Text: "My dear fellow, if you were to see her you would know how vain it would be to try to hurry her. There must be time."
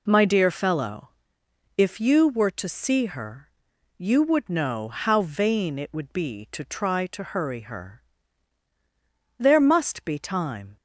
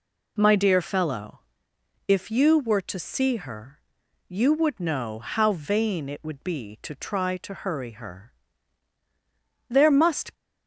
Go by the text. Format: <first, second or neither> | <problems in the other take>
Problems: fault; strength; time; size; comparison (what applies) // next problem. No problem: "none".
first | pauses between "her" and "you"; noticeable; at 3.7 s; 0.50 s long; noticeable in the first // stops before "be time"; at 10.3 s